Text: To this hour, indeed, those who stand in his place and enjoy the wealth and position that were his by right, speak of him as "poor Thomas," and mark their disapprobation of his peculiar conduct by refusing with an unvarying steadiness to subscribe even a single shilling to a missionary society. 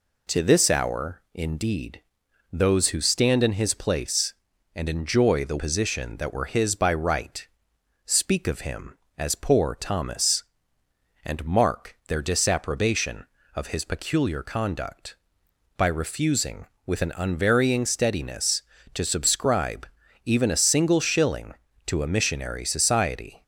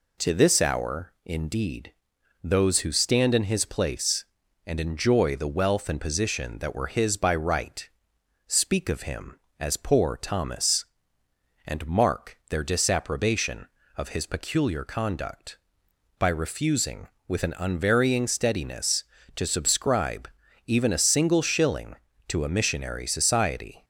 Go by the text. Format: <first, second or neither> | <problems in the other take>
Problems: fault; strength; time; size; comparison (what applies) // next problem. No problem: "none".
second | skips "wealth and"; at 5.5 s // pauses between "subscribe" and "even"; at 19.8 s; 0.38 s long; also in the second